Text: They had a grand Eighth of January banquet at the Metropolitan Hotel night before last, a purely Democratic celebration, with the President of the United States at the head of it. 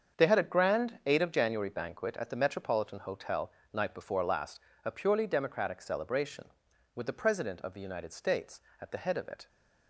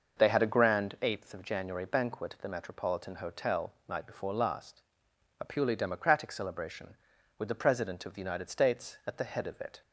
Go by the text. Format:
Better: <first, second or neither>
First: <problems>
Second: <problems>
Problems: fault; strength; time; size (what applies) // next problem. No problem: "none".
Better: second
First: starts louder than the rest; until 1.2 s; 7 dB // says "Eight" for "Eighth"; at 1.0 s // pauses between "Hotel" and "night"; slight; at 3.4 s; 0.22 s long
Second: pauses between "Hotel" and "night"; slight; at 3.7 s; 0.16 s long